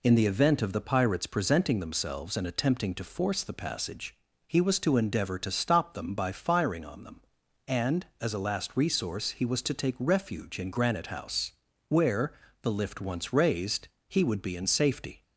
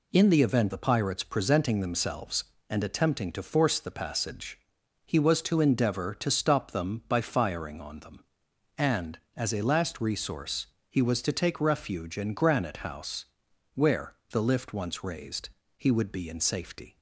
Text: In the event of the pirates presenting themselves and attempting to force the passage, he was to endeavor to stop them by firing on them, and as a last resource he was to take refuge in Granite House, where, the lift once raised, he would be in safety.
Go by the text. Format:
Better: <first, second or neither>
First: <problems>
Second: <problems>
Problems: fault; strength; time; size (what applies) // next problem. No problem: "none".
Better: first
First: none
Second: skips "of"; at 0.7 s // pauses between "resource" and "he"; slight; at 10.6 s; 0.24 s long